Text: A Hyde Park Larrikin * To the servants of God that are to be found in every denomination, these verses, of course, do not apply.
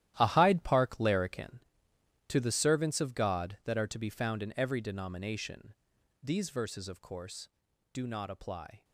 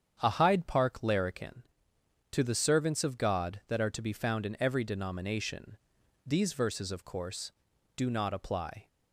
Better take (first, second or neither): second